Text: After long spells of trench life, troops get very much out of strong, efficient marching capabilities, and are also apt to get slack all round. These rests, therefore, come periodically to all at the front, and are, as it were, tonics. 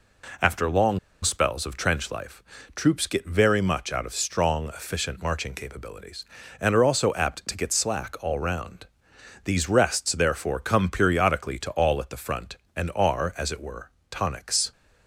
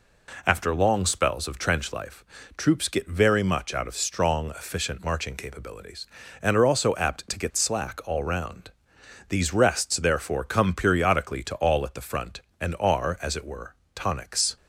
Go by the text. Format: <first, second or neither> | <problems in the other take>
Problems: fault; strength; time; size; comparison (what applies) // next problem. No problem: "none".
second | pauses between "long" and "spells"; slight; at 0.9 s; 0.24 s long